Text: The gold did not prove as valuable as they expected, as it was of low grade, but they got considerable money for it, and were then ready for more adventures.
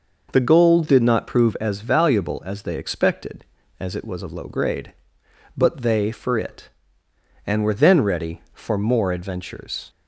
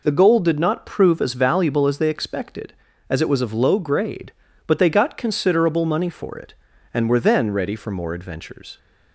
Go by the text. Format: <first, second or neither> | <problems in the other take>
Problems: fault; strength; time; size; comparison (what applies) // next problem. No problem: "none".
second | skips "got considerable money"; at 6.1 s